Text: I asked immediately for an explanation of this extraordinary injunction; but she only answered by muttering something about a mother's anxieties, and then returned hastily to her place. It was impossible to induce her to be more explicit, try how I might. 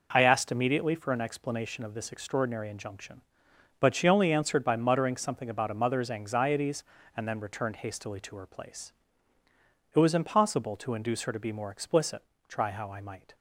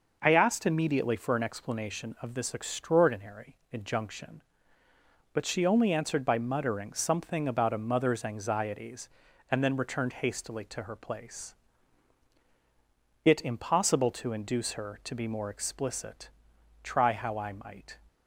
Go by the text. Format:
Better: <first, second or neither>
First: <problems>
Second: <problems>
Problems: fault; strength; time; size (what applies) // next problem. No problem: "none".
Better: first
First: none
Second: pauses between "extraordinary" and "injunction"; slight; at 3.5 s; 0.16 s long // skips "was"; at 13.4 s